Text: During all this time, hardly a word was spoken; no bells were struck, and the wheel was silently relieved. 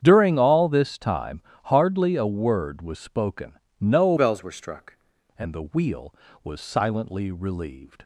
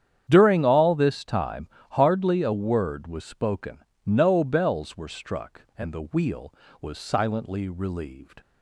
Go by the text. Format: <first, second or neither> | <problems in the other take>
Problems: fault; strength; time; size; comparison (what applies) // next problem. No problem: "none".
second | starts louder than the rest; strong; until 1.0 s; 8.5 dB; strong in the second // changes voice from "bells" to "struck"; from 4.1 to 4.9 s; 0.8 s long